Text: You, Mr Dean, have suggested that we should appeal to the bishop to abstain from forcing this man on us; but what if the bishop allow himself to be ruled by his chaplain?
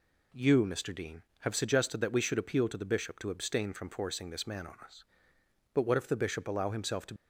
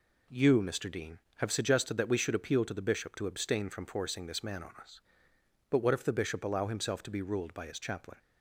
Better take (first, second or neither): second